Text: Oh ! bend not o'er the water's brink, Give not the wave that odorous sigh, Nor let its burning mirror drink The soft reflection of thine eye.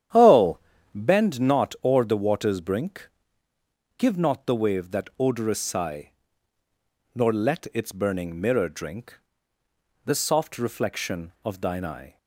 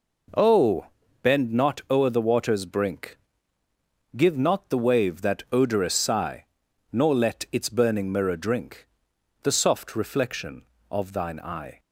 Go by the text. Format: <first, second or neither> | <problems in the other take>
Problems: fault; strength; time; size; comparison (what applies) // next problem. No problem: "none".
second | starts louder than the rest; strong; until 1.3 s; 10 dB // pauses between "drink" and "The"; noticeable; at 9.1 s; 0.86 s long; noticeable in the second